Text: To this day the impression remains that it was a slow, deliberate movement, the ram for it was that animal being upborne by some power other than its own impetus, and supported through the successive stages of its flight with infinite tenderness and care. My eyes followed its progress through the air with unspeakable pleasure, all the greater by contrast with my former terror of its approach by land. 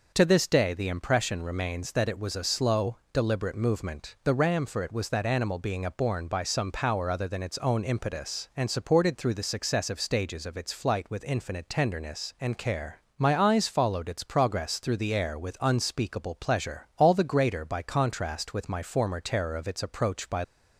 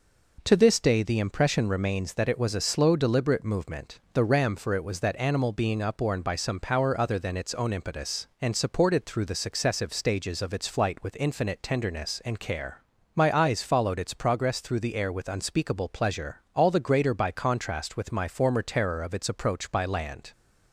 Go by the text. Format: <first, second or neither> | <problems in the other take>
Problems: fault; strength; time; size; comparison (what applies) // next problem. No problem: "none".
second | stops before "land"; at 20.4 s